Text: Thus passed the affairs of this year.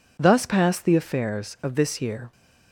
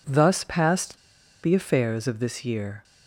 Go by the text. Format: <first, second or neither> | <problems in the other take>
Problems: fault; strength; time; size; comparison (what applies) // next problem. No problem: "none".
first | pauses between "passed" and "the"; at 0.9 s; 0.45 s long